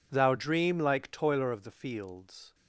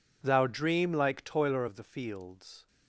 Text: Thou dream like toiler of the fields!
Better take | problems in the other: neither | none

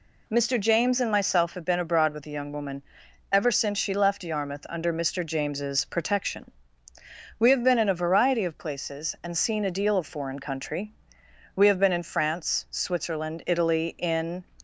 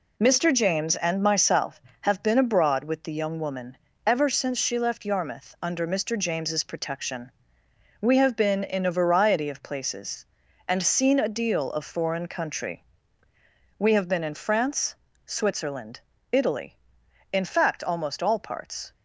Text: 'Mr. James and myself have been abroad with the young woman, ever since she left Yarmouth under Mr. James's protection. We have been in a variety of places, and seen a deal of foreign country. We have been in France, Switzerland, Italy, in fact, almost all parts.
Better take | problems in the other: second | stops before "fact almost all parts"; at 14.5 s

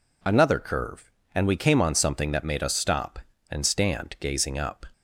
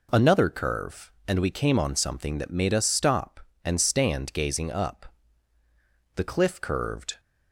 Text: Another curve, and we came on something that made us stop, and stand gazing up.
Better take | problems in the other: first | goes on to say "The cliff curved"; noticeable; from 6.1 s on; 1.0 s long

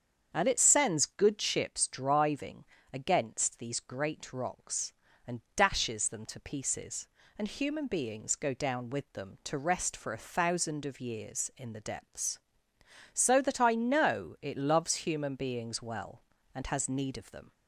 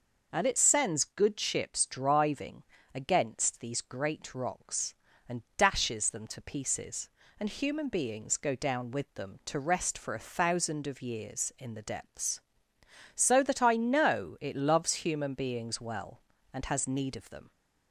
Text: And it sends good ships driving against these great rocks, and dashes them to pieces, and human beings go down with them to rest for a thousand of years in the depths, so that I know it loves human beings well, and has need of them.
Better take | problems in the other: second | starts louder than the rest; strong; until 1.8 s; 7.5 dB // pauses between "driving" and "against"; slight; at 2.6 s; 0.30 s long; slight in the second

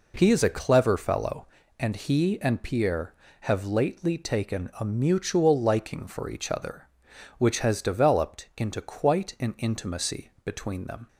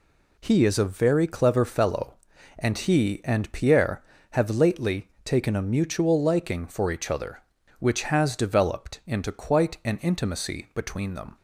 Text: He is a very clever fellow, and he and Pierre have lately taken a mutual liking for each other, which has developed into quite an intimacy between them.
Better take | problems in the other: second | skips "very"; at 0.5 s

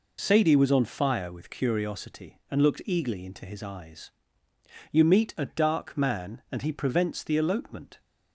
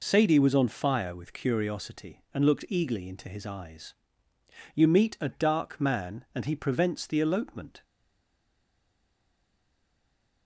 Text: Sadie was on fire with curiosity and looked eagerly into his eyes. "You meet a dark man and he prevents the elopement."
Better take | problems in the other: first | stays silent after the last word; strong; from 7.8 s on; 2.6 s long

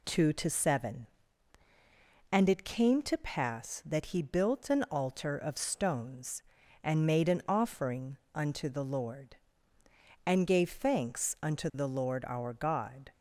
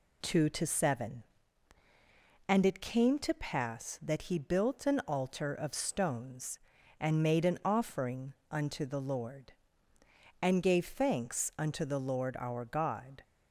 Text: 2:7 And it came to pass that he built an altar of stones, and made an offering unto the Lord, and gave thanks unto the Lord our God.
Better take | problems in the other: neither | pauses between "offering" and "unto"; slight; the same in both

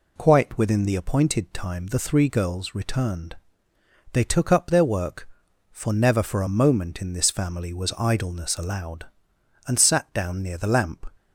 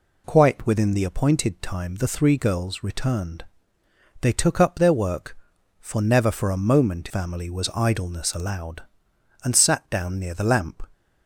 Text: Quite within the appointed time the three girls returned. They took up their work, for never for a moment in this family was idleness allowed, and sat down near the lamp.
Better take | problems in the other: first | skips "in this"; at 7.0 s

